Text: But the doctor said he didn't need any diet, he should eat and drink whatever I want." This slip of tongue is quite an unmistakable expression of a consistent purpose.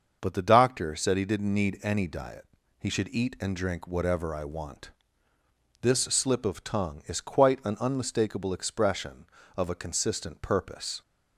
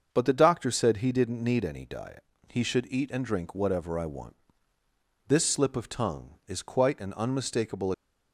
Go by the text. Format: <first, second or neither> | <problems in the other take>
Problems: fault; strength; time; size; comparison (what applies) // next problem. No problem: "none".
first | starts louder than the rest; until 1.1 s; 6.5 dB; also in the first // stops before "expression of a consistent purpose"; at 7.9 s